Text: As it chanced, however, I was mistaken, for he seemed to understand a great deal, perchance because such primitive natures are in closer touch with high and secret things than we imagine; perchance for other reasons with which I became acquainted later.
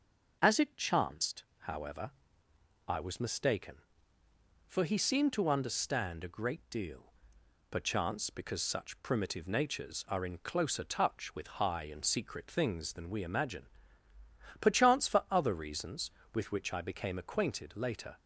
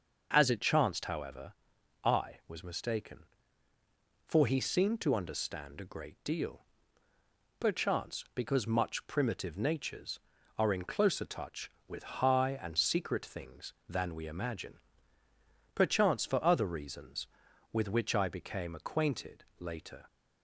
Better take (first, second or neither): first